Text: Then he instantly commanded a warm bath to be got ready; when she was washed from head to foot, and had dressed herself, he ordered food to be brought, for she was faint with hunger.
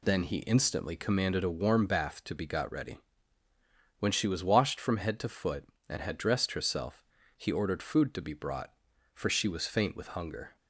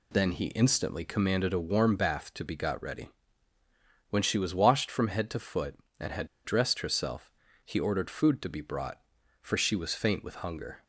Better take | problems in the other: first | pauses between "had" and "dressed"; slight; at 6.2 s; 0.17 s long

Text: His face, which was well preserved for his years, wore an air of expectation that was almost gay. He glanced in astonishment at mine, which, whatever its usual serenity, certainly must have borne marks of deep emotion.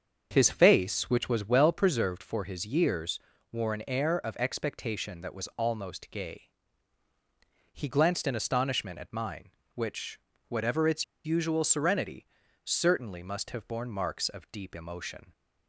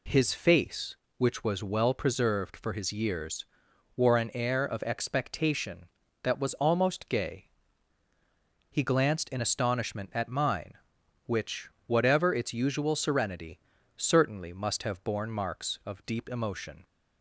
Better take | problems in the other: second | starts louder than the rest; until 1.3 s; 6.5 dB // pauses between "its" and "usual"; slight; at 11.0 s; 0.20 s long

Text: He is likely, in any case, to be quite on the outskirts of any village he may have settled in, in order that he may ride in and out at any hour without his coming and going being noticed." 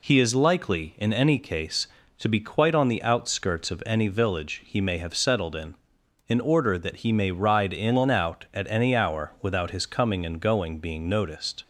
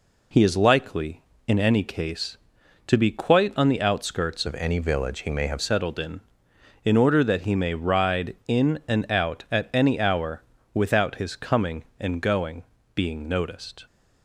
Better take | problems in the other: first | changes voice from "of" to "have"; from 4.4 to 5.5 s; 1.1 s long // pauses between "hour" and "without"; slight; at 10.4 s; 0.30 s long // pauses between "going" and "being"; slight; at 12.6 s; 0.32 s long

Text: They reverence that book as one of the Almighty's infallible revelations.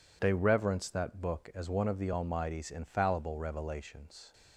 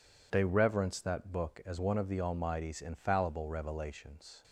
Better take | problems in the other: neither | none

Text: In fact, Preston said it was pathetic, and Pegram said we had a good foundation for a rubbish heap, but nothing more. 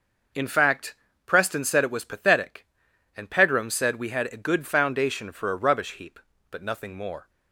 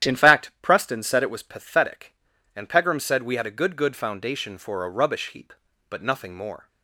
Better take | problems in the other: first | starts louder than the rest; strong; until 1.1 s; 10.5 dB // says "good" twice; at 3.7 s

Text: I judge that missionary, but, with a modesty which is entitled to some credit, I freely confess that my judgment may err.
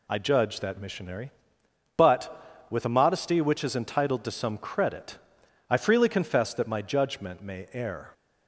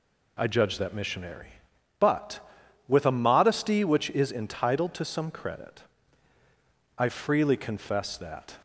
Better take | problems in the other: first | stops before "my judgment may err"; at 8.5 s

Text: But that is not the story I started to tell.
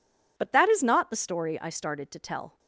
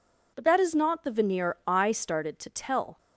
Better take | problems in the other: first | says "veneer" for "story"; at 1.1 s

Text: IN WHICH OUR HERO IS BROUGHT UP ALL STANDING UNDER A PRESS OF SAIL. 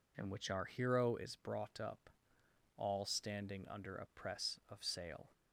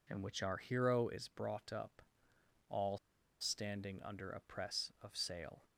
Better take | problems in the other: first | pauses between "UP" and "ALL"; noticeable; at 1.9 s; 0.70 s long; noticeable in the first // pauses between "ALL" and "STANDING"; at 2.9 s; 0.44 s long

